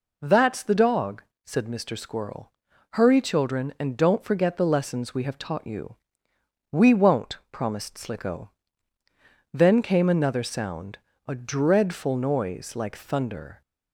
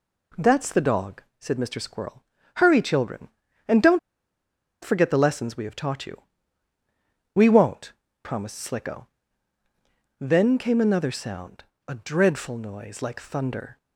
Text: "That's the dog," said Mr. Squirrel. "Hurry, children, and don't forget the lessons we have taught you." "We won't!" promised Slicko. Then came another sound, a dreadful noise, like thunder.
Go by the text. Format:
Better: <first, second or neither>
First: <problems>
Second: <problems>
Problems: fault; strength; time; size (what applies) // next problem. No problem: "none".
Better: first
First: none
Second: pauses between "don't" and "forget"; noticeable; at 3.9 s; 0.83 s long